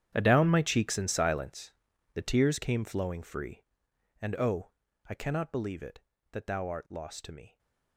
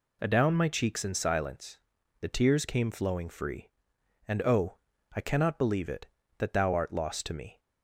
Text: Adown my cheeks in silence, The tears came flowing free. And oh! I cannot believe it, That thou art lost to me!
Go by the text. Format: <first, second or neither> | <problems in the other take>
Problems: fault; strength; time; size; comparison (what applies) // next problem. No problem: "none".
second | gets quieter; strong; throughout; 16.5 dB